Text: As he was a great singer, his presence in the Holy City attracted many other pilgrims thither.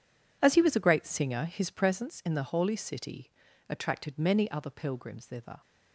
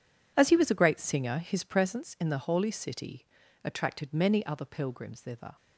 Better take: neither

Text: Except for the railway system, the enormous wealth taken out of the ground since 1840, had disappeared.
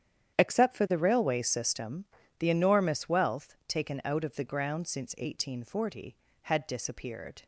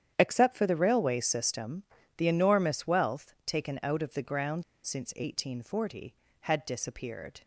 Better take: first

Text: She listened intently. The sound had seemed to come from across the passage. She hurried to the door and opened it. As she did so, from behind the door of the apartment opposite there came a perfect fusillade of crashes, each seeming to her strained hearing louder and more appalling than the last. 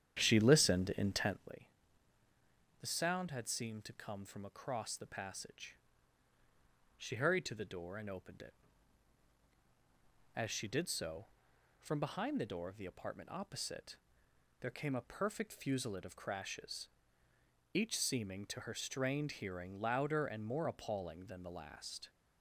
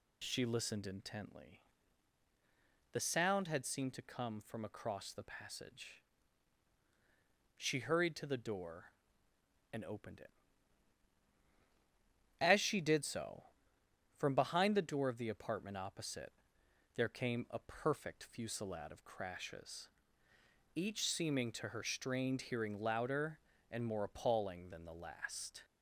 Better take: second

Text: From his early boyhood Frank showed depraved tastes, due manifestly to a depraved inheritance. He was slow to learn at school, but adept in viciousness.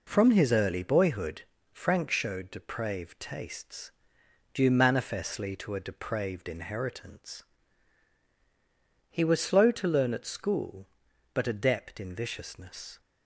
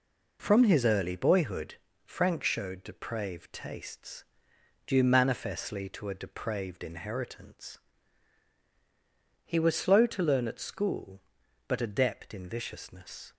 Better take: neither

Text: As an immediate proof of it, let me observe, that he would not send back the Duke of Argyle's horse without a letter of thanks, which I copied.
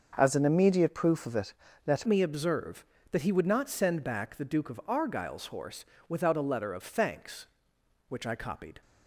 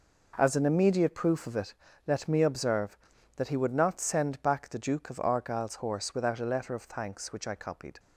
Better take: second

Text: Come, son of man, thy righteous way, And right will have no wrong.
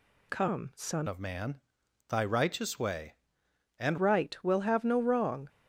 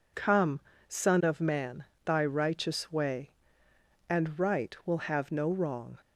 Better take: second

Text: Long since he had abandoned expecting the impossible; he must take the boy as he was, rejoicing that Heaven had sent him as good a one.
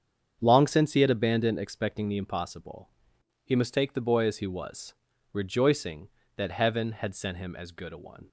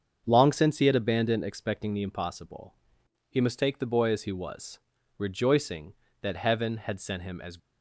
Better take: first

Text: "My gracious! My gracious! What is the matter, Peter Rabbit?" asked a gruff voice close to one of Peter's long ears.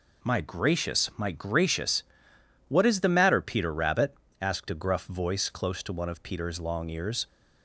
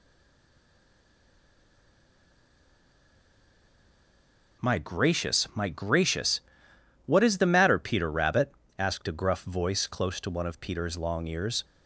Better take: first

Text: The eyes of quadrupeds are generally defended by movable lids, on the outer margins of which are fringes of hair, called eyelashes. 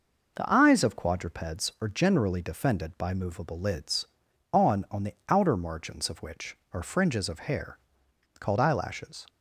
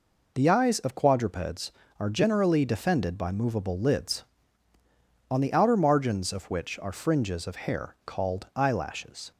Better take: second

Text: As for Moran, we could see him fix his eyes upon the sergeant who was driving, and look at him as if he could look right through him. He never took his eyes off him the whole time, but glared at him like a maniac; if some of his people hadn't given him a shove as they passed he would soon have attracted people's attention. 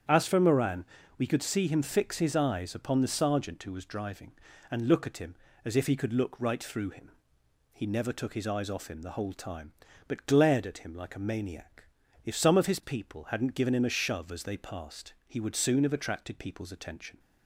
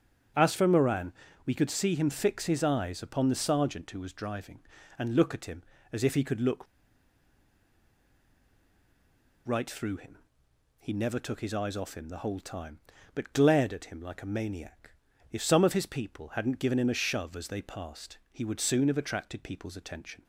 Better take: first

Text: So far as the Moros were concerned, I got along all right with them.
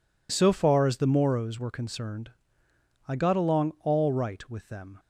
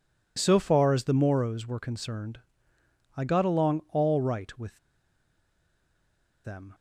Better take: first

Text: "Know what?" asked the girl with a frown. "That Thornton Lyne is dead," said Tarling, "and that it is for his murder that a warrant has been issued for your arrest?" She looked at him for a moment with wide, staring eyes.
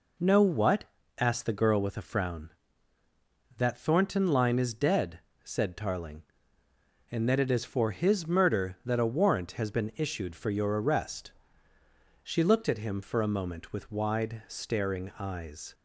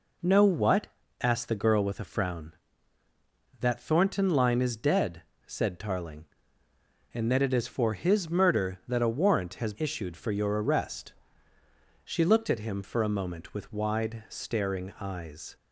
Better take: first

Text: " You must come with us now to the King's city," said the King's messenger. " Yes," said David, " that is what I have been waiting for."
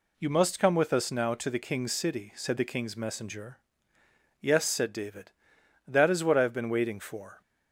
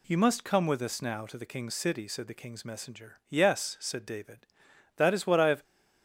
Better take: first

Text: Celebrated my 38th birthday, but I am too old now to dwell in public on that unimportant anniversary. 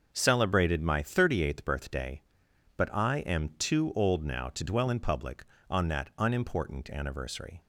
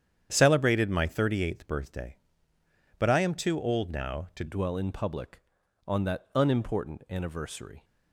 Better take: first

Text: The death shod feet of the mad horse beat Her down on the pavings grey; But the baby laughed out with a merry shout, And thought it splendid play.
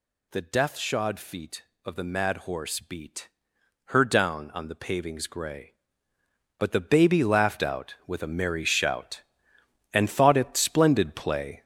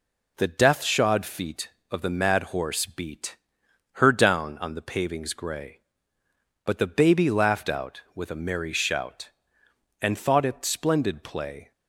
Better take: second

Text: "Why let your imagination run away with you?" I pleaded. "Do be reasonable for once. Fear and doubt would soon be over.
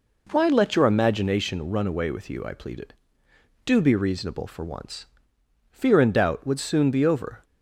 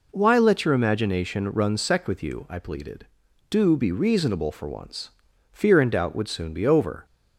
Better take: first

